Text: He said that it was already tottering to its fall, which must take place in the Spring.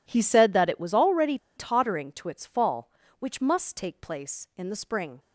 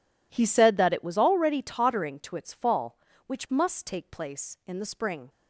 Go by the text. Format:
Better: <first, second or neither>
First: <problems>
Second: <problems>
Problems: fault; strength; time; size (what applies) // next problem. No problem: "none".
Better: second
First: pauses between "already" and "tottering"; slight; at 1.3 s; 0.19 s long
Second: none